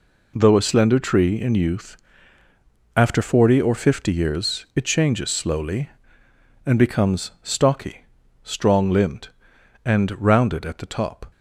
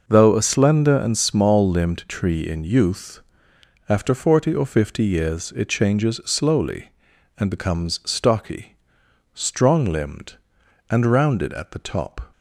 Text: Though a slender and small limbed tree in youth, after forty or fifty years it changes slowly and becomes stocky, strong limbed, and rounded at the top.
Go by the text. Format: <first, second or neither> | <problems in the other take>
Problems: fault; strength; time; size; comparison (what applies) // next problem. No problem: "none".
second | skips "and small limbed"; at 0.9 s